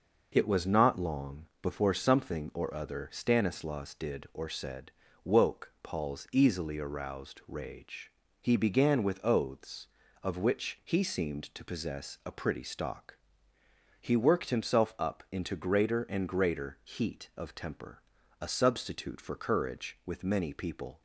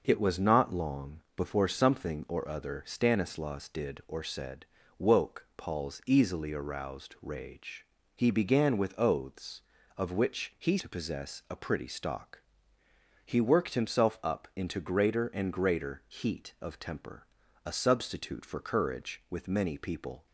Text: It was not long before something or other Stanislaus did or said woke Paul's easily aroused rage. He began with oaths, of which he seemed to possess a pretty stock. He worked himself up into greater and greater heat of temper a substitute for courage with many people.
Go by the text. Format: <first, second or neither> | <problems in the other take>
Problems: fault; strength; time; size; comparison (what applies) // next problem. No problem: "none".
first | pauses between "said" and "woke"; slight; at 4.6 s; 0.36 s long; slight in the first // skips "seemed"; at 10.7 s // pauses between "temper" and "a"; at 17.2 s; 0.40 s long; also in the first